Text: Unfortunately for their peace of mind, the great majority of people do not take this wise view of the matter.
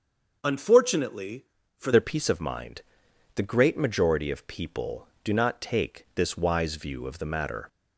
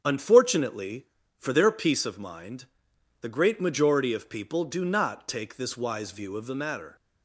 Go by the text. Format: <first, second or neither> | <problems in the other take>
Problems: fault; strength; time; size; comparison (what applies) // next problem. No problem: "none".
second | starts louder than the rest; until 1.4 s; 6.5 dB; strong in the second // changes voice at "their"; from 1.9 s on; 5.7 s long